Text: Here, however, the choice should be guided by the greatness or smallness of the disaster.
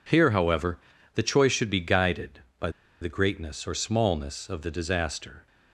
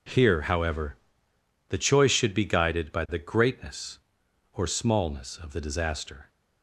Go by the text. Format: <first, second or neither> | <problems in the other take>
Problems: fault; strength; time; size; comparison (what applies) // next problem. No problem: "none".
second | pauses between "by" and "the"; slight; at 2.7 s; 0.30 s long